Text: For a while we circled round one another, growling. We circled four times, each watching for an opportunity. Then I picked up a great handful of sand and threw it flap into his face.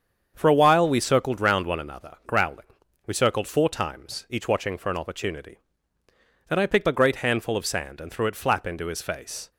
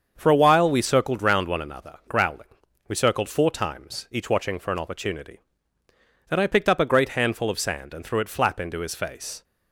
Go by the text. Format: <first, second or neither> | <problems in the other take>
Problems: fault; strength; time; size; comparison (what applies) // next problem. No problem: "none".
second | starts louder than the rest; strong; until 1.3 s; 7.5 dB; also in the second // skips "up"; at 6.8 s